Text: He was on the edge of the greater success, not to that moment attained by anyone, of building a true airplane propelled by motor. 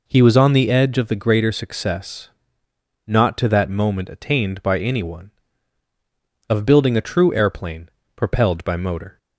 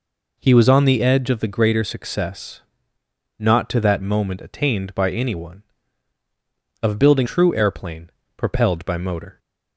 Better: first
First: pauses between "airplane" and "propelled"; slight; at 7.8 s; 0.26 s long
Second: skips "a"; at 7.2 s // pauses between "airplane" and "propelled"; slight; at 8.1 s; 0.26 s long

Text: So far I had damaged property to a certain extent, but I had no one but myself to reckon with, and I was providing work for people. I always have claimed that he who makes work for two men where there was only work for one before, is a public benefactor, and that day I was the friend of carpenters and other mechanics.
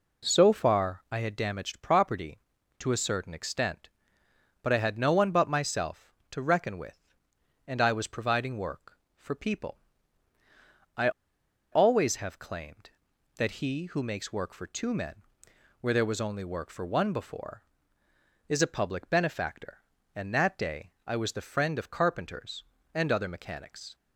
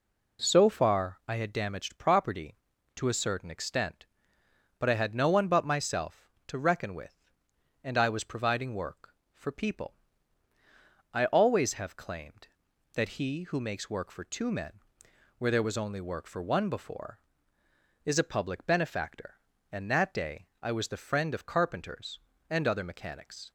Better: second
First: pauses between "I" and "always"; noticeable; at 11.0 s; 0.62 s long // pauses between "men" and "where"; noticeable; at 15.1 s; 0.64 s long // pauses between "day" and "I"; slight; at 20.9 s; 0.16 s long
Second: pauses between "men" and "where"; noticeable; at 14.7 s; 0.64 s long // pauses between "day" and "I"; slight; at 20.4 s; 0.16 s long

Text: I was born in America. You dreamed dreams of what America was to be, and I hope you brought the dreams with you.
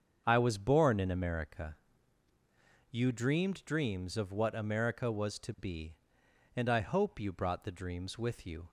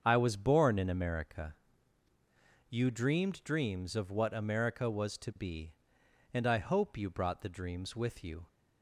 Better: neither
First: starts louder than the rest; strong; until 1.2 s; 7 dB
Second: starts louder than the rest; strong; until 1.0 s; 7 dB

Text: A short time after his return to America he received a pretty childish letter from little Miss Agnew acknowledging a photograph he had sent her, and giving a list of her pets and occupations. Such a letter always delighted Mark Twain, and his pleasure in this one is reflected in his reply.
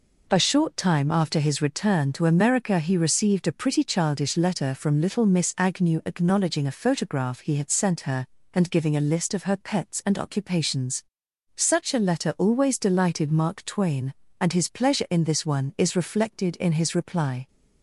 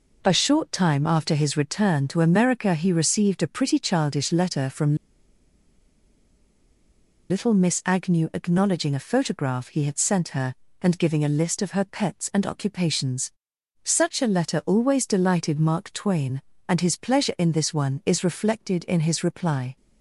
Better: first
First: none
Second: pauses between "from" and "little"; strong; at 4.9 s; 2.3 s long

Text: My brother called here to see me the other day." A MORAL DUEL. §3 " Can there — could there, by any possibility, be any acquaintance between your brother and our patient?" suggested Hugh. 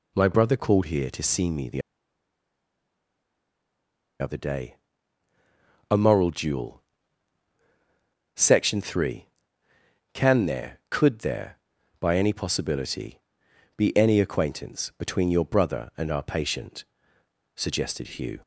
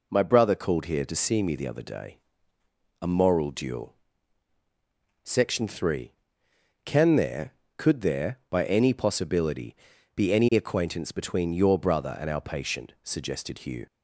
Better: second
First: pauses between "the" and "other"; strong; at 1.8 s; 2.3 s long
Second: none

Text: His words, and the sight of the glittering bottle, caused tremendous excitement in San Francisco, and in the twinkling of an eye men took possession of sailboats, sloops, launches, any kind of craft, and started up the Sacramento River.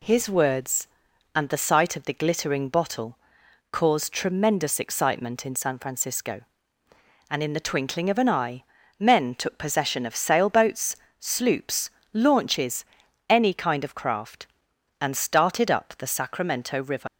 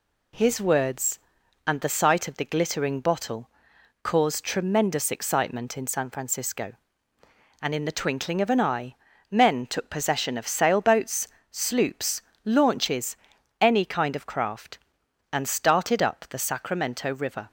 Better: second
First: pauses between "eye" and "men"; slight; at 8.6 s; 0.34 s long // leaves "River" unfinished; at 17.0 s; 110 ms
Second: pauses between "eye" and "men"; slight; at 8.9 s; 0.34 s long

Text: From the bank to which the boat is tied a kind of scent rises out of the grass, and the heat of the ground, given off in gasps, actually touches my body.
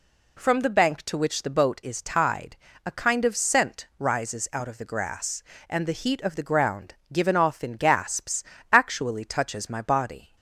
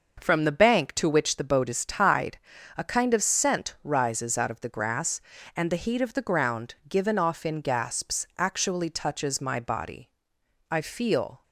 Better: first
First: pauses between "tied" and "a"; slight; at 2.5 s; 0.30 s long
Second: starts louder than the rest; noticeable; until 1.2 s; 6 dB // pauses between "tied" and "a"; at 2.3 s; 0.38 s long // goes on to say "I feel"; noticeable; from 10.7 s on; 0.72 s long

